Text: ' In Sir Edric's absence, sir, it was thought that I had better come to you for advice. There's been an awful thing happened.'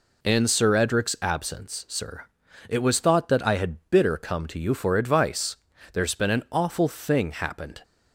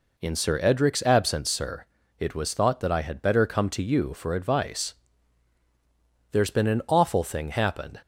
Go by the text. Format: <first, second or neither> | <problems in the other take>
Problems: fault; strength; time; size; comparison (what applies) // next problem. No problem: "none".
second | says "bitter" for "better"; at 3.8 s